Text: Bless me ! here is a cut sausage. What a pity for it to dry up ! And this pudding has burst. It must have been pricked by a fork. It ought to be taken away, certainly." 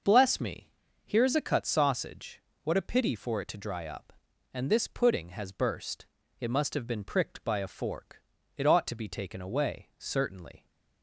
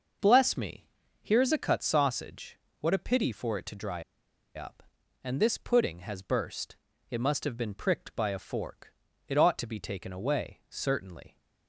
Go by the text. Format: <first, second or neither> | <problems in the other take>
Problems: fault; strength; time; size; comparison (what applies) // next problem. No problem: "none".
first | pauses between "dry" and "up"; noticeable; at 4.0 s; 0.53 s long